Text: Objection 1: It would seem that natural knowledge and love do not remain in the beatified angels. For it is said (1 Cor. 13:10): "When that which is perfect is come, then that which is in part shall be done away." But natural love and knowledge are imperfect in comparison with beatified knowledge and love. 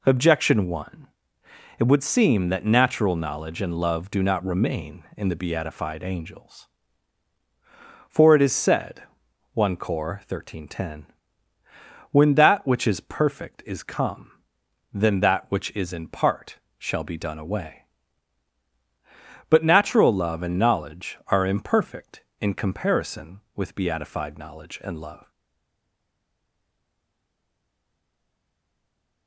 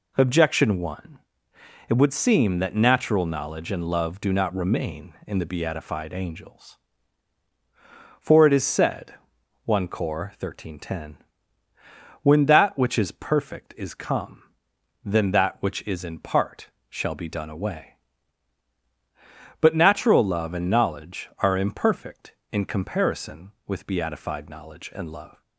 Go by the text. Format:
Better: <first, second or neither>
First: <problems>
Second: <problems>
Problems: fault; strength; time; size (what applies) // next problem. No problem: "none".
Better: second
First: pauses between "part" and "shall"; slight; at 16.5 s; 0.22 s long // stays silent after the last word; strong; from 25.3 s on; 3.9 s long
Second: pauses between "part" and "shall"; slight; at 16.6 s; 0.22 s long